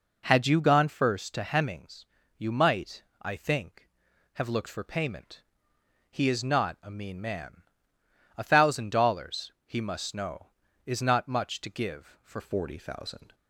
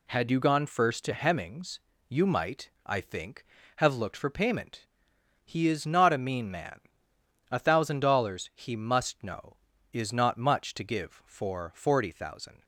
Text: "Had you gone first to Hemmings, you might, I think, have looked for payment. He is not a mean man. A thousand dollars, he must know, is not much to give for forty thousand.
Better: second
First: changes voice at "forty"; from 12.3 s on; 1.0 s long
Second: none

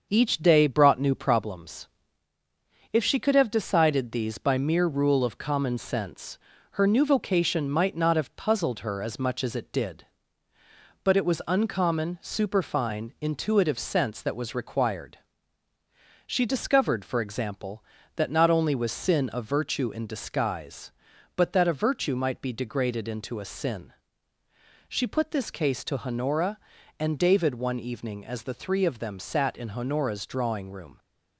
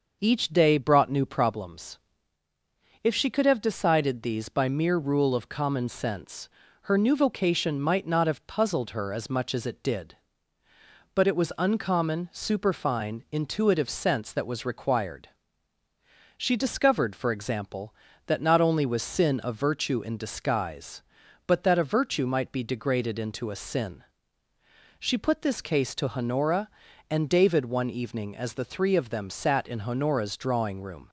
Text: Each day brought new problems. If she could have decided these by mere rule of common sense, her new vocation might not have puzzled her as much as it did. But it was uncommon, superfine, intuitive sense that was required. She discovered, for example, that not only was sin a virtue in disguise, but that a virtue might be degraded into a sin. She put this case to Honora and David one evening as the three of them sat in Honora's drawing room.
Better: second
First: gets quieter; throughout; 4 dB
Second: none

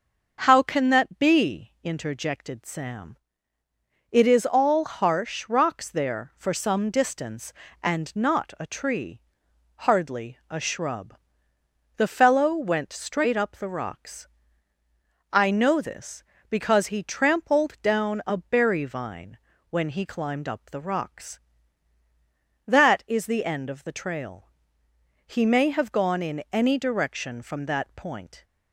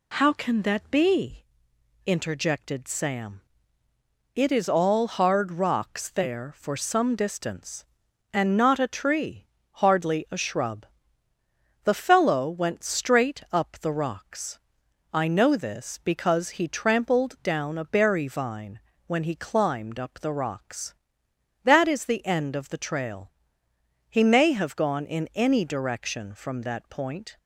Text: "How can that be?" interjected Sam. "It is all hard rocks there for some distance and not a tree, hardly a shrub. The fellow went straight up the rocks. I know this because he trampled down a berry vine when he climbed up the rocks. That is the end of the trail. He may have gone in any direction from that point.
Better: second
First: starts louder than the rest; noticeable; until 1.4 s; 6 dB // says "harsh" for "hard"; at 4.8 s // pauses between "vine" and "when"; slight; at 19.3 s; 0.32 s long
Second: pauses between "vine" and "when"; slight; at 18.8 s; 0.27 s long

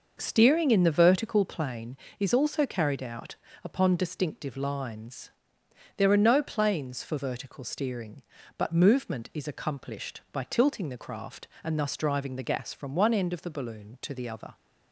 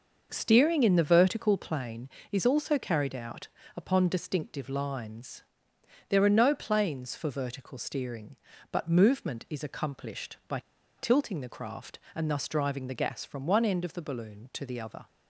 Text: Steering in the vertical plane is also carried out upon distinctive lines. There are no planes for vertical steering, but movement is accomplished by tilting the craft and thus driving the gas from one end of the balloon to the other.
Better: first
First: pauses between "out" and "upon"; slight; at 3.3 s; 0.26 s long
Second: pauses between "out" and "upon"; slight; at 3.4 s; 0.26 s long // pauses between "by" and "tilting"; at 10.6 s; 0.37 s long

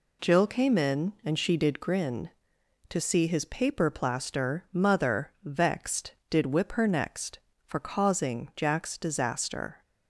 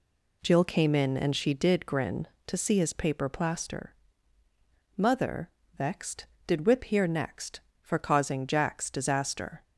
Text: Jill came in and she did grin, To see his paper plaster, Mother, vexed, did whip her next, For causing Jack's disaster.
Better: first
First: none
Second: says "here" for "her"; at 6.8 s

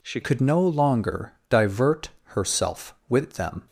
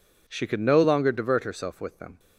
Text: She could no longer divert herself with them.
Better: second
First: changes voice at "could"; from 0.2 s on; 3.4 s long // pauses between "longer" and "divert"; slight; at 1.3 s; 0.16 s long // pauses between "divert" and "herself"; slight; at 2.1 s; 0.16 s long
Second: none

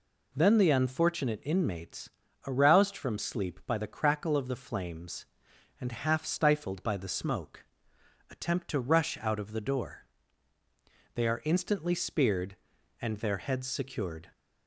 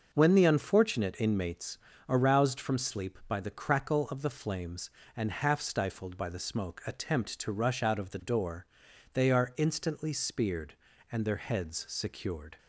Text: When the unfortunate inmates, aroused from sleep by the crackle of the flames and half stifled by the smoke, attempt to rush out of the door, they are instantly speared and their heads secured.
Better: second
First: says "Then" for "When"; at 0.3 s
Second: none

